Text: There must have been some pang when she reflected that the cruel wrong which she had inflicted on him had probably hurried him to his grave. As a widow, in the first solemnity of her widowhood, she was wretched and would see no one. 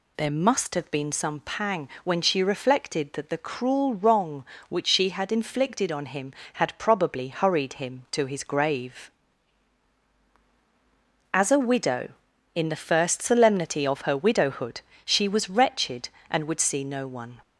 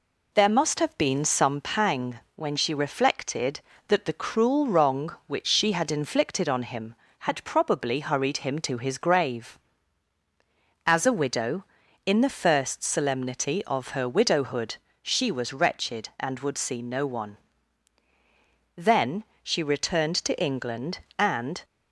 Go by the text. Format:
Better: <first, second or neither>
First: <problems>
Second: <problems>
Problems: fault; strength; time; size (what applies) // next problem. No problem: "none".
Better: first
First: none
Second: pauses between "pang" and "when"; slight; at 2.2 s; 0.16 s long // goes on to say "Then she returned to England and"; strong; from 18.7 s on; 2.8 s long